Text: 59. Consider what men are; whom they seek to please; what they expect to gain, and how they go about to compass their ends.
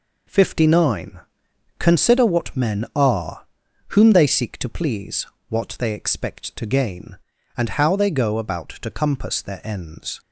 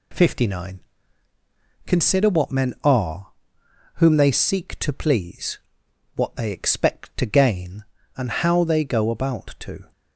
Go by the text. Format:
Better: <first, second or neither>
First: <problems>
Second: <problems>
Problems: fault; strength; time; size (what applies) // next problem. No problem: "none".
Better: first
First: none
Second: stops before "compass their ends"; at 9.9 s